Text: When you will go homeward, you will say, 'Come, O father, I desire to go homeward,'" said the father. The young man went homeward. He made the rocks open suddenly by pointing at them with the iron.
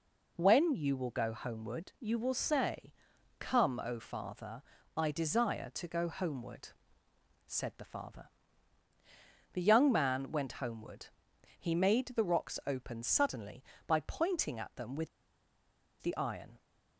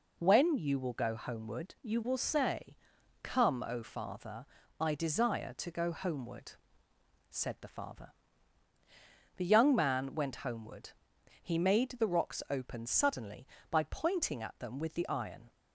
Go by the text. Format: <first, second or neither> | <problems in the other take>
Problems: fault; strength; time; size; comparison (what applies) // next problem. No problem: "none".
second | pauses between "with" and "the"; noticeable; at 15.0 s; 0.93 s long